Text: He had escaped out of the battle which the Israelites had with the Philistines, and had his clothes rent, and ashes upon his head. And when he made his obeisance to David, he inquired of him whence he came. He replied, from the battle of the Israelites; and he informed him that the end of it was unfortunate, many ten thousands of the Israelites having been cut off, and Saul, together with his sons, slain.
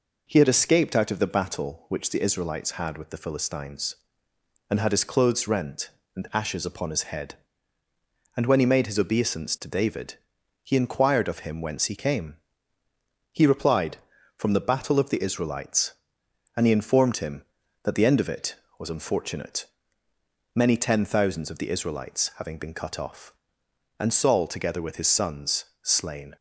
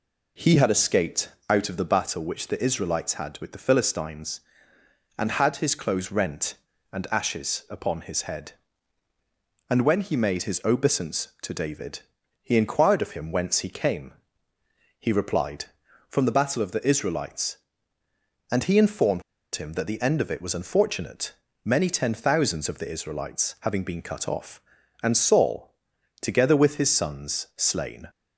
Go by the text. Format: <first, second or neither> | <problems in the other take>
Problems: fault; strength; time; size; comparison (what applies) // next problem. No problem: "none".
first | pauses between "escaped" and "out"; slight; at 1.3 s; 0.18 s long // pauses between "informed" and "him"; slight; at 19.2 s; 0.32 s long